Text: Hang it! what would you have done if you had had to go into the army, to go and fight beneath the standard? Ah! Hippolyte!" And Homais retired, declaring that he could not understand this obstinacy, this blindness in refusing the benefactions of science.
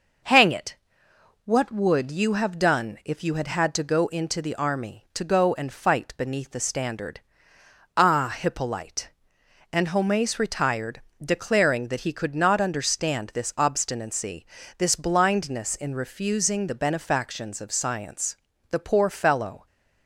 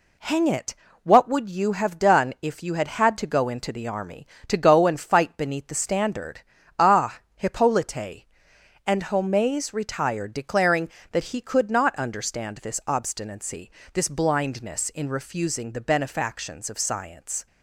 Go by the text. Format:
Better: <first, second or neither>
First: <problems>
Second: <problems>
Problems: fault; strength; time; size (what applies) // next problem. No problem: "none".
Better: second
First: goes on to say "The poor fellow"; noticeable; from 18.6 s on; 0.96 s long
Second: none